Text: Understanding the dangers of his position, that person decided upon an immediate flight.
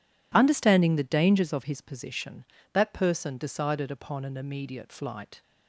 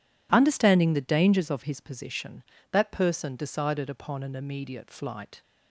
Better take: neither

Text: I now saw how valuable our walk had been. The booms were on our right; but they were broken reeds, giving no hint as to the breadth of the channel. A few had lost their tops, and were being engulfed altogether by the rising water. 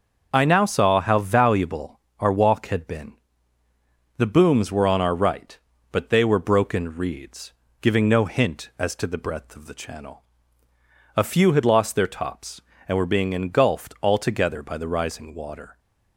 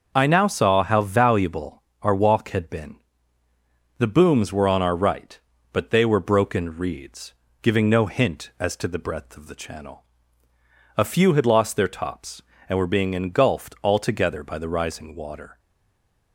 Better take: first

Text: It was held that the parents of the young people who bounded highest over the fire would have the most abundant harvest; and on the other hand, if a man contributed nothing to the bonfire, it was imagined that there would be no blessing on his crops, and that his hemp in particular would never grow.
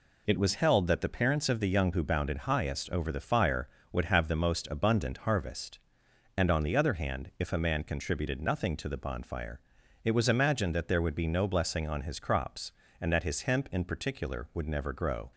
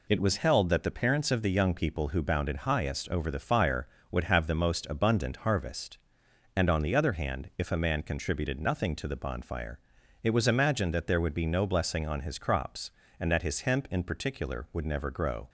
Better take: second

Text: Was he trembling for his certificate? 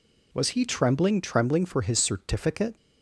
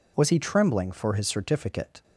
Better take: second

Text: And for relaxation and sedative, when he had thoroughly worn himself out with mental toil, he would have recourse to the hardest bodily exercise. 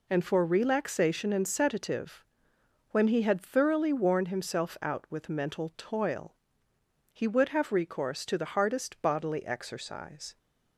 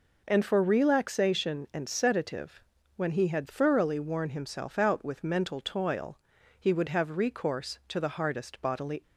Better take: first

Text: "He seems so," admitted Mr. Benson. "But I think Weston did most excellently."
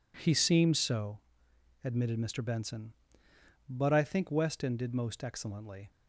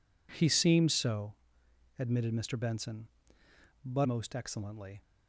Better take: first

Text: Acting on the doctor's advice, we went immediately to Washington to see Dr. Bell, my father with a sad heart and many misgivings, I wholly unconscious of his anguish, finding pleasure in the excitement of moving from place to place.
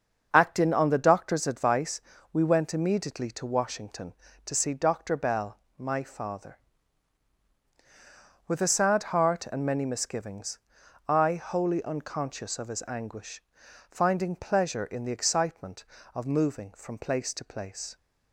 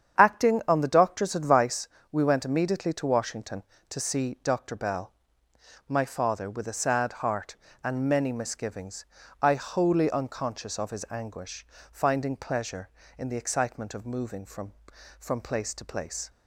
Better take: first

